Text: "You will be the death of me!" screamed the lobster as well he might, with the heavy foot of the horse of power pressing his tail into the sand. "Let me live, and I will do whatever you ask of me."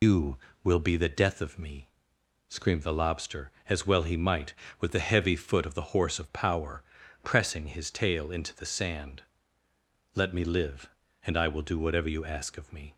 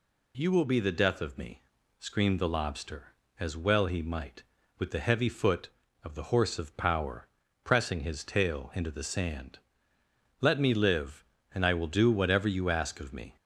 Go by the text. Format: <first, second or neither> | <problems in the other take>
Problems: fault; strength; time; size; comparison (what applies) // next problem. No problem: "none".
second | loses the start of "You"; at 0.0 s; 145 ms // pauses between "power" and "pressing"; at 6.8 s; 0.40 s long; also in the second